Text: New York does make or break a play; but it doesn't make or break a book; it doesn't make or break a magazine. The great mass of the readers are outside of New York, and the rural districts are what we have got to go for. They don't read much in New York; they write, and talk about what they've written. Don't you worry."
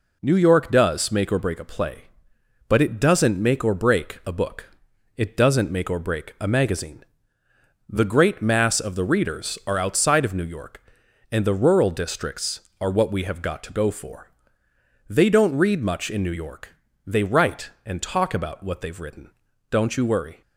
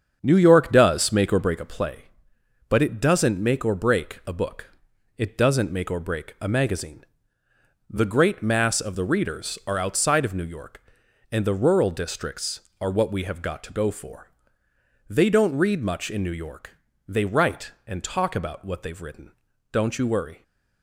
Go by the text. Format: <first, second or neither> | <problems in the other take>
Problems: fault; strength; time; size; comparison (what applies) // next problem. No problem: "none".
first | starts louder than the rest; strong; until 1.9 s; 7.5 dB